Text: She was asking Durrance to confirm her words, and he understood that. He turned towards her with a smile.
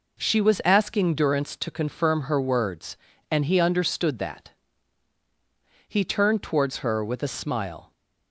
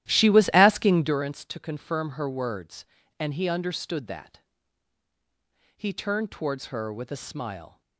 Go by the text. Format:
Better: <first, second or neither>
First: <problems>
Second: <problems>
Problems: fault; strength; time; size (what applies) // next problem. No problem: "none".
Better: first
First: none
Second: starts louder than the rest; strong; until 1.2 s; 13 dB